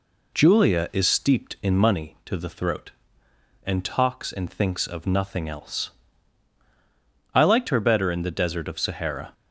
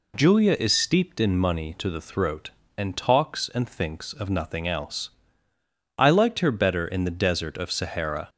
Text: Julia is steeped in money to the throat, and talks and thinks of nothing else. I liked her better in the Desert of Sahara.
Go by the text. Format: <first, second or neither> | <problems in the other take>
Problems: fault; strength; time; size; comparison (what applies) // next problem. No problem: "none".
neither | none